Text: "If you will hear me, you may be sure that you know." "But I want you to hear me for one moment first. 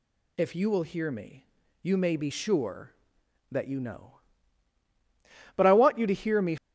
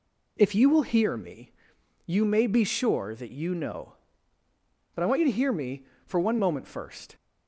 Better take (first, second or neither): second